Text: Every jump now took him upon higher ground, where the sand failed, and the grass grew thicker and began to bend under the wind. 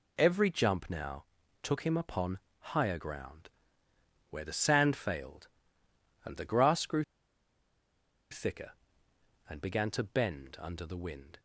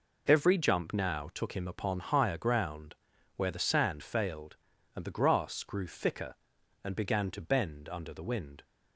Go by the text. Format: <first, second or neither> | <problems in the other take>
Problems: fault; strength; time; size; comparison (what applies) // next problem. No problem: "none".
second | pauses between "now" and "took"; slight; at 1.2 s; 0.36 s long // pauses between "upon" and "higher"; slight; at 2.3 s; 0.20 s long // pauses between "grew" and "thicker"; strong; at 7.0 s; 1.2 s long